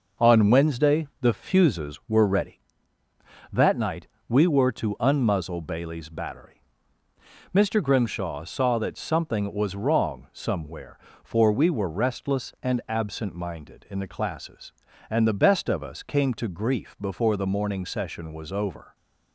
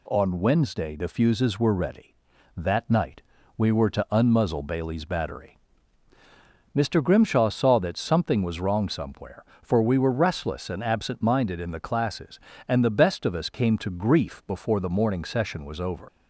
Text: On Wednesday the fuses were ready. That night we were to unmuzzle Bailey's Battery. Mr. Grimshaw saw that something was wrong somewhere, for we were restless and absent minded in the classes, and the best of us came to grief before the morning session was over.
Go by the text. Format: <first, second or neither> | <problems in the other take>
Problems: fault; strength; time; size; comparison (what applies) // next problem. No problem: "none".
first | pauses between "night" and "we"; slight; at 3.2 s; 0.34 s long; slight in the first // leaves "over" unfinished; at 16.0 s; 80 ms